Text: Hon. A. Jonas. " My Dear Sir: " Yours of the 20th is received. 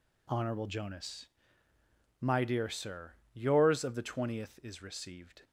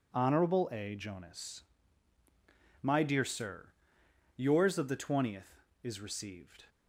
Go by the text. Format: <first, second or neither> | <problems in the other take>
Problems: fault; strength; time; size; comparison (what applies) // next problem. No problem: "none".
second | skips "A"; at 0.6 s